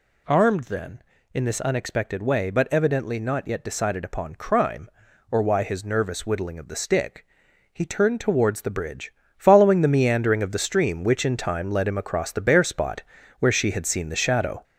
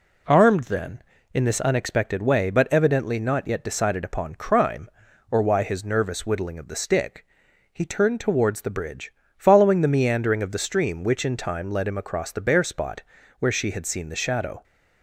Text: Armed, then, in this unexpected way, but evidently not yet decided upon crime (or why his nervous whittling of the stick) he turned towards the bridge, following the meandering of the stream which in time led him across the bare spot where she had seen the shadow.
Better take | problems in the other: second | gets louder; noticeable; throughout; 4.5 dB // pauses between "spot" and "where"; slight; at 13.0 s; 0.34 s long; slight in the second

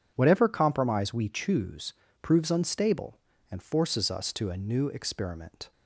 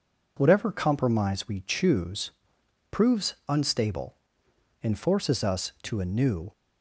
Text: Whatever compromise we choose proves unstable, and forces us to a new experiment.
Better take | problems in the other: first | pauses between "choose" and "proves"; noticeable; at 2.2 s; 0.62 s long; slight in the first // stops before "experiment"; at 6.5 s

